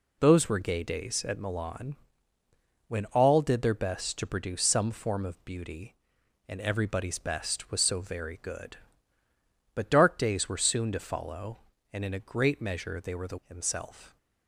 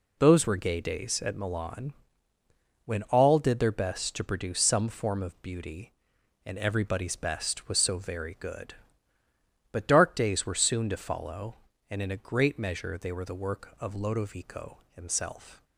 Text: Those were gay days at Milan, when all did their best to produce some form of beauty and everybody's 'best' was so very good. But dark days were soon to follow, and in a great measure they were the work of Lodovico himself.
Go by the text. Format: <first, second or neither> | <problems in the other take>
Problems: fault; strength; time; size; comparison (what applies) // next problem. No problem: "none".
second | skips "work of Lodovico"; at 13.4 s